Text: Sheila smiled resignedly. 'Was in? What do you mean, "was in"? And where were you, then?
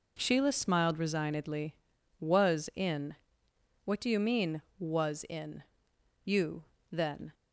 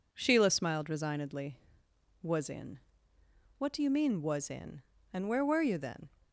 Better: second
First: skips "And where were"; at 5.9 s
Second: none

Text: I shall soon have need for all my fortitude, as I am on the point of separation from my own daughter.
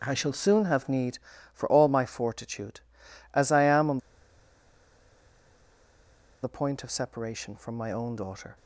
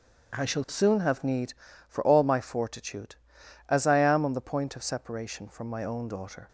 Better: second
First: starts louder than the rest; strong; until 1.0 s; 7.5 dB // pauses between "on" and "the"; strong; at 3.9 s; 2.4 s long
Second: starts louder than the rest; strong; until 1.4 s; 8 dB

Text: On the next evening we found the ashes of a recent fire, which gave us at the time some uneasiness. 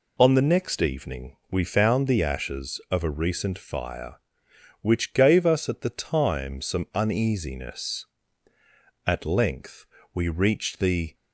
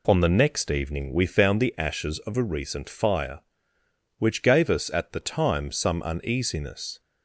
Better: second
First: goes on to say "At length we reached the"; strong; from 9.0 s on; 2.0 s long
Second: none

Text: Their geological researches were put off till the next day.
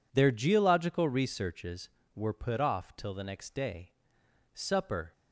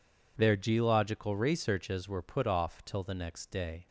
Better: second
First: goes on to say "Supper"; from 4.5 s on; 0.58 s long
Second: none

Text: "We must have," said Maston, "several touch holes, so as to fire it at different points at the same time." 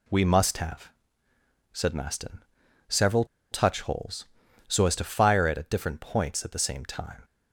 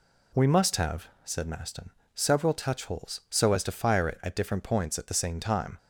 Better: second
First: pauses between "several" and "touch"; slight; at 3.2 s; 0.27 s long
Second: none

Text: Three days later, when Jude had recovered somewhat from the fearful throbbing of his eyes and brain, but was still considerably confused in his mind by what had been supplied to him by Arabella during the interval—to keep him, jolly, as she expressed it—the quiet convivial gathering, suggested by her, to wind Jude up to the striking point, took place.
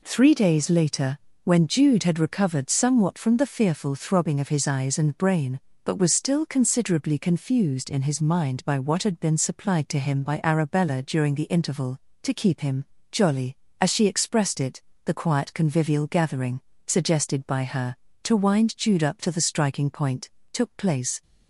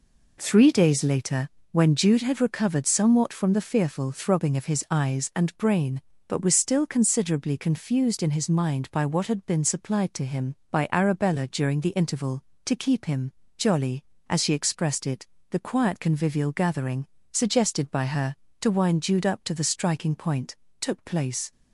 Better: neither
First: none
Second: none

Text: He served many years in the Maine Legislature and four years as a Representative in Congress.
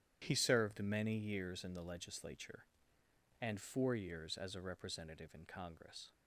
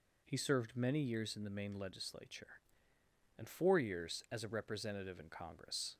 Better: second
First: starts louder than the rest; strong; until 1.2 s; 11 dB // skips "Maine"; at 1.8 s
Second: none

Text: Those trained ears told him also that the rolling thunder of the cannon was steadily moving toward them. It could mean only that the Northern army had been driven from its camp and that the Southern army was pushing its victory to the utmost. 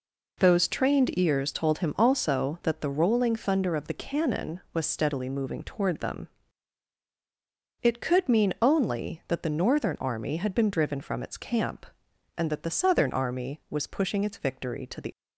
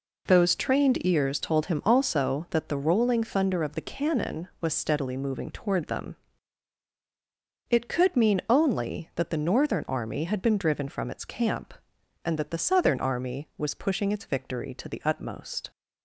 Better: second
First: stops before "utmost"; at 15.1 s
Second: none

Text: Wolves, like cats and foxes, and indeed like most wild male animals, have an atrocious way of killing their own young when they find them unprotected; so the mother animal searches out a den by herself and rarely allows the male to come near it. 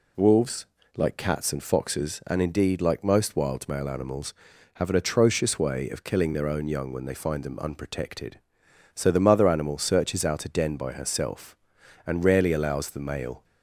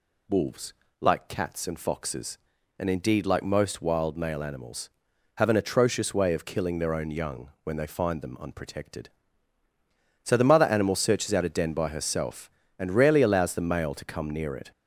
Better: second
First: stops before "to come near it"; at 13.4 s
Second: none

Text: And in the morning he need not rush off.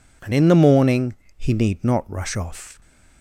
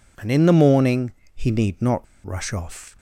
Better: first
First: pauses between "morning" and "he"; slight; at 1.1 s; 0.22 s long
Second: pauses between "morning" and "he"; slight; at 1.1 s; 0.22 s long // pauses between "not" and "rush"; slight; at 2.0 s; 0.19 s long

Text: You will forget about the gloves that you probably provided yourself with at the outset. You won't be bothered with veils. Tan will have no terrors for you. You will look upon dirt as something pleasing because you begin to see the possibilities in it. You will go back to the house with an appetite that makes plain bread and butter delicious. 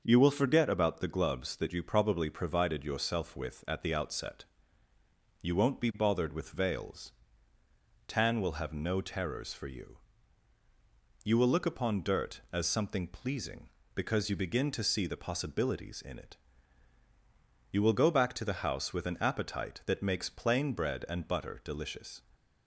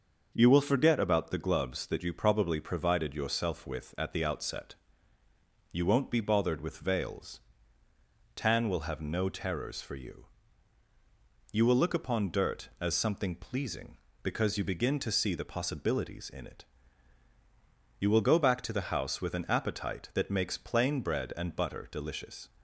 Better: neither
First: starts louder than the rest; until 1.0 s; 6 dB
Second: starts louder than the rest; until 1.3 s; 6.5 dB

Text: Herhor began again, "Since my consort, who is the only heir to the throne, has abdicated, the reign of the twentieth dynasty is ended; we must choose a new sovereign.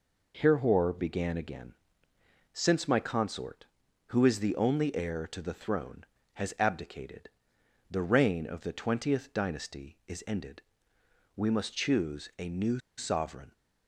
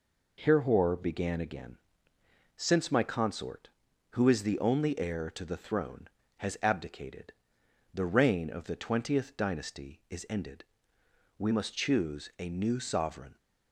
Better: second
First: pauses between "new" and "sovereign"; slight; at 12.7 s; 0.17 s long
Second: none

